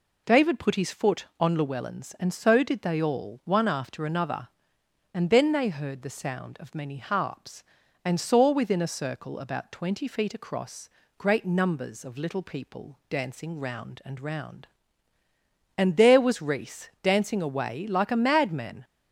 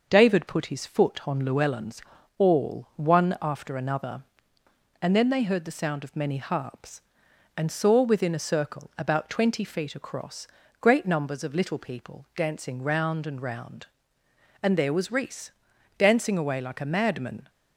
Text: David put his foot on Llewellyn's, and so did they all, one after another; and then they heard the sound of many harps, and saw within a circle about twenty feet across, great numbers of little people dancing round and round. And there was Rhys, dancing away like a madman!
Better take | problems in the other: first | starts louder than the rest; until 1.1 s; 6 dB // skips "and so did they"; at 2.1 s

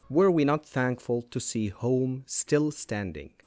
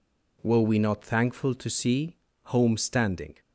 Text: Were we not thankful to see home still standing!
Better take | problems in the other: first | pauses between "see" and "home"; slight; at 2.1 s; 0.28 s long // skips "still"; at 2.7 s

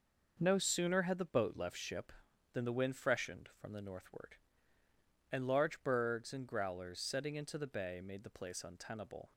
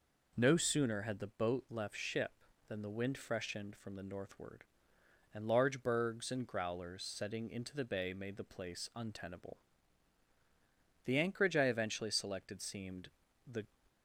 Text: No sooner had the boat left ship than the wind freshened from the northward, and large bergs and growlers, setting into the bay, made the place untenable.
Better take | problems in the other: first | goes on to say "The anchorage I eventually selected seemed the"; strong; from 11.0 s on; 2.6 s long

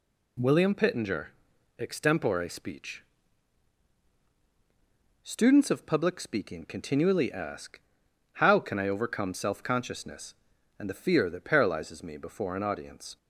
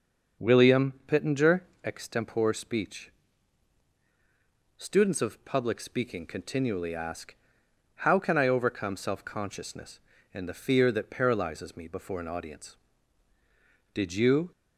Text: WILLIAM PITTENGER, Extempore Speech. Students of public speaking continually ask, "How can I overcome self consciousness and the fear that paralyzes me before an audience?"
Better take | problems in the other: first | starts louder than the rest; until 1.5 s; 6 dB // pauses between "WILLIAM" and "PITTENGER"; slight; at 0.9 s; 0.16 s long // goes on to say "Did you"; from 13.9 s on; 0.57 s long

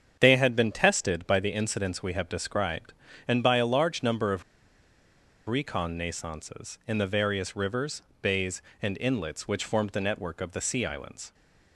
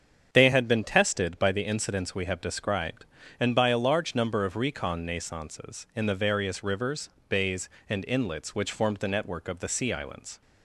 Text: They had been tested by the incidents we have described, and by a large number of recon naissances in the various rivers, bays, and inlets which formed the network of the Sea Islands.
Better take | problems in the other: second | starts louder than the rest; strong; until 1.2 s; 7.5 dB; strong in the second // pauses between "of" and "recon"; at 4.4 s; 1.0 s long

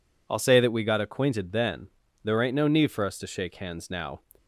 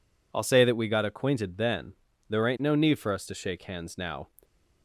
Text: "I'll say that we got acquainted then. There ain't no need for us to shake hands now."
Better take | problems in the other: neither | none

